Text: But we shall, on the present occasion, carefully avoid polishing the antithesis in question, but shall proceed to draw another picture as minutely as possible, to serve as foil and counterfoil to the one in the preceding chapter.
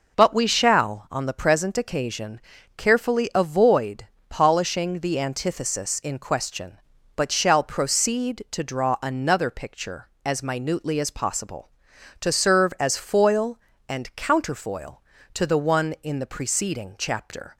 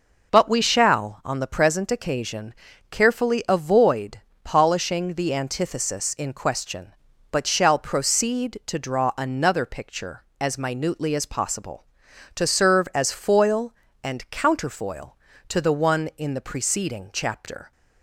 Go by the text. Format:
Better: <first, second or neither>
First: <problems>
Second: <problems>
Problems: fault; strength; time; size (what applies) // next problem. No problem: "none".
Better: neither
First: pauses between "avoid" and "polishing"; slight; at 4.0 s; 0.23 s long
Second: pauses between "avoid" and "polishing"; slight; at 4.1 s; 0.24 s long